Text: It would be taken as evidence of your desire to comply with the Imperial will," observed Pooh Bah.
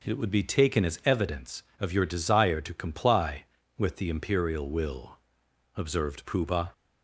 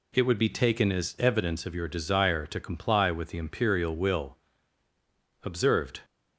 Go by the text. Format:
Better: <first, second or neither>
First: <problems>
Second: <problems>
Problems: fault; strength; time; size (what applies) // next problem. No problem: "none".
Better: first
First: none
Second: stops before "Pooh Bah"; at 6.0 s